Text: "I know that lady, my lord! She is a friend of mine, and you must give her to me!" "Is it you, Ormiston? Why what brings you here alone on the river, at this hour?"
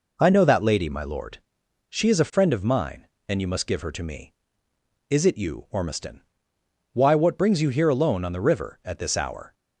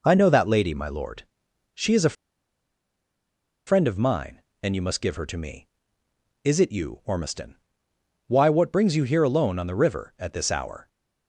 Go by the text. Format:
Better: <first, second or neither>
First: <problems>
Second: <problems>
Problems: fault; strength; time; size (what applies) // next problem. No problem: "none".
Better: first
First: none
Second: pauses between "a" and "friend"; strong; at 2.1 s; 1.5 s long